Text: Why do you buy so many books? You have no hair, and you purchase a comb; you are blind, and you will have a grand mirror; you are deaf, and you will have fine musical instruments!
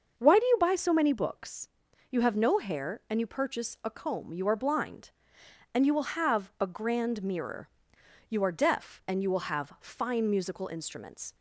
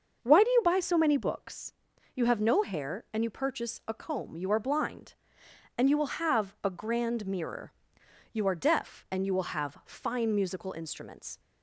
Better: neither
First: starts louder than the rest; until 1.2 s; 6.5 dB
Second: starts louder than the rest; until 1.2 s; 6 dB

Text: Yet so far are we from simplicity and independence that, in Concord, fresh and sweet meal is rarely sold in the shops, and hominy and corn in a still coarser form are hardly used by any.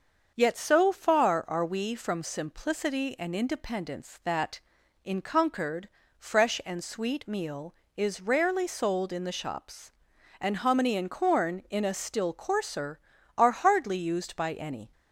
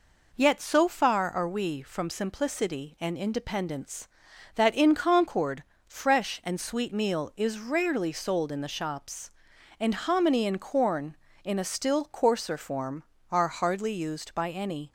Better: second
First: starts louder than the rest; until 1.3 s; 6.5 dB // skips "form"; at 13.1 s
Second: none

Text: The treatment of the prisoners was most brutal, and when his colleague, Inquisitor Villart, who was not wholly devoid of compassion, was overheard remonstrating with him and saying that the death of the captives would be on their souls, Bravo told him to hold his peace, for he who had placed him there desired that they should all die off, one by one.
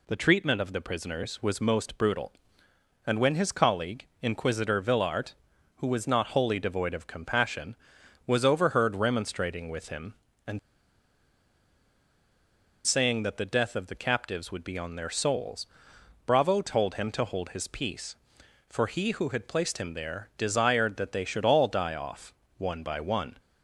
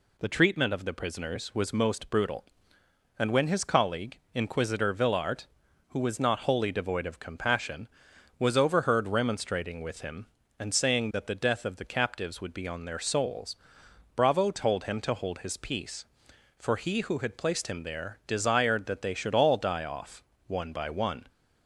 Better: second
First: pauses between "and" and "saying"; strong; at 10.5 s; 2.2 s long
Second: none

